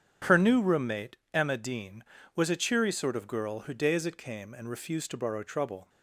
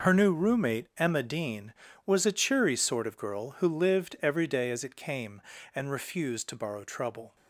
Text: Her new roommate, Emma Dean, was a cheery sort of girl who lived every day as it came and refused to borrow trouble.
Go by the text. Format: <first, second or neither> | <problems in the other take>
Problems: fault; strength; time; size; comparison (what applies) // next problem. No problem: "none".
second | starts louder than the rest; strong; until 1.4 s; 8.5 dB // skips "lived every"; at 3.7 s